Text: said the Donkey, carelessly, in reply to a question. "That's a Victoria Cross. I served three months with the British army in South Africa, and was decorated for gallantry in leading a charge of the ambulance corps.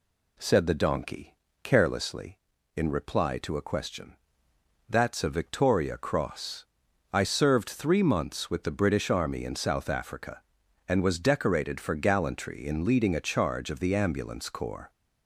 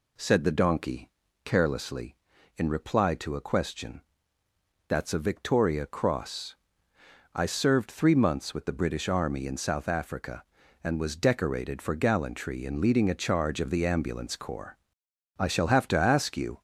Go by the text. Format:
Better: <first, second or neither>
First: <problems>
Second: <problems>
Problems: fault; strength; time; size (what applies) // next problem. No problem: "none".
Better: first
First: none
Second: goes on to say "I shall have to ask you"; noticeable; from 15.3 s on; 1.2 s long